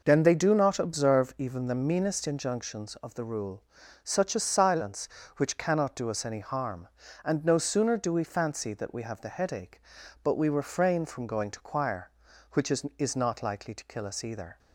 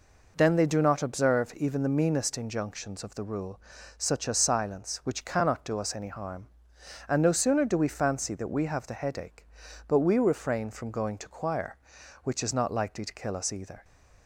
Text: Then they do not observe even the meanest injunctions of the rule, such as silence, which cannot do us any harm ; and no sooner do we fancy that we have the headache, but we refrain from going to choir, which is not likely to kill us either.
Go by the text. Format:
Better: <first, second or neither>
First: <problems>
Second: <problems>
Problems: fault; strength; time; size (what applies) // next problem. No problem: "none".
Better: second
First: says "is" twice; at 12.9 s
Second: none